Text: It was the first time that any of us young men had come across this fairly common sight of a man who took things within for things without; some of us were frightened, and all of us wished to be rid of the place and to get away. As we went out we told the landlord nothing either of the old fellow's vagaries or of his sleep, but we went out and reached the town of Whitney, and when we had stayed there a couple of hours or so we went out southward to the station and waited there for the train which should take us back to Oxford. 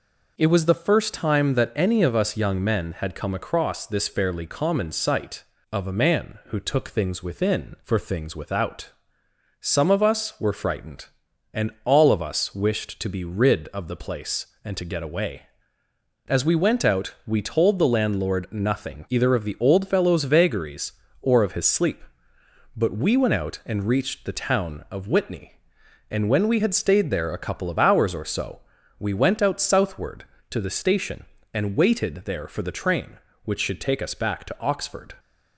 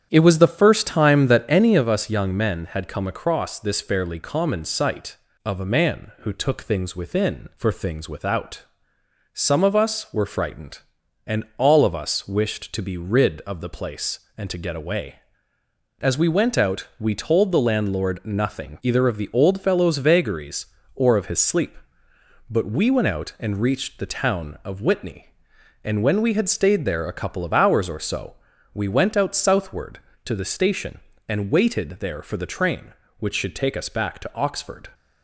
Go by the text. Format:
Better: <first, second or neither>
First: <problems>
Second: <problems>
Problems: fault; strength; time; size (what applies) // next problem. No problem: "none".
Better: first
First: pauses between "so" and "we"; at 28.5 s; 0.40 s long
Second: starts louder than the rest; strong; until 1.8 s; 9 dB // pauses between "so" and "we"; at 28.3 s; 0.40 s long